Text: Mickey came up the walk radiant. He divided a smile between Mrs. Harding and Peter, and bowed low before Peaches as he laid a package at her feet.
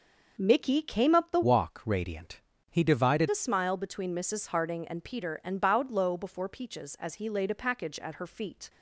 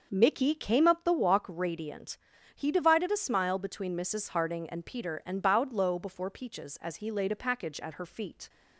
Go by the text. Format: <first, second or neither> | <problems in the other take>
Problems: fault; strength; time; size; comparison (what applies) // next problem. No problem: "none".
second | starts louder than the rest; until 1.3 s; 6 dB; also in the second // changes voice from "walk" to "divided"; from 1.4 to 3.2 s; 1.8 s long